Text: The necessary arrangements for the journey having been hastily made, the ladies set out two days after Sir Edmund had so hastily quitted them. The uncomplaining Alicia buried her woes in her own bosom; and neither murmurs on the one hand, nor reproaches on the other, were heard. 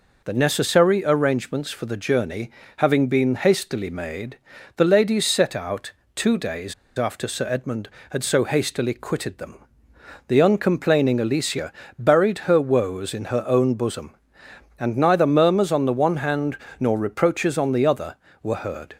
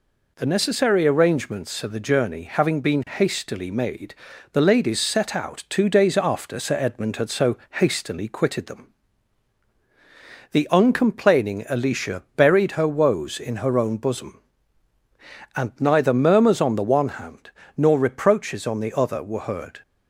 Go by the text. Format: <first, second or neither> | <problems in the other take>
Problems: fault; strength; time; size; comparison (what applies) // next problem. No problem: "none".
second | pauses between "journey" and "having"; slight; at 2.4 s; 0.28 s long // pauses between "out" and "two"; slight; at 5.9 s; 0.24 s long // pauses between "days" and "after"; slight; at 6.7 s; 0.24 s long // pauses between "Alicia" and "buried"; slight; at 11.7 s; 0.24 s long